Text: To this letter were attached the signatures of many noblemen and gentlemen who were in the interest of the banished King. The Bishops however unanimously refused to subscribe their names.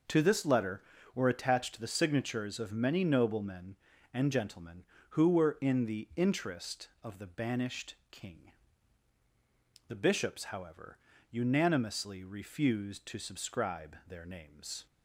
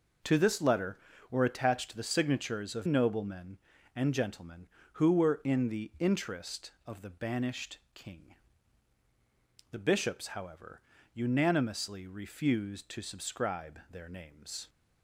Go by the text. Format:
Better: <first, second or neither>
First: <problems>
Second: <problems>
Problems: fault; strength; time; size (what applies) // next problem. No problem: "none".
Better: first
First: pauses between "banished" and "King"; slight; at 7.9 s; 0.16 s long // pauses between "however" and "unanimously"; slight; at 10.9 s; 0.34 s long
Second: skips "many"; at 2.8 s // pauses between "banished" and "King"; slight; at 7.7 s; 0.16 s long // pauses between "however" and "unanimously"; slight; at 10.8 s; 0.34 s long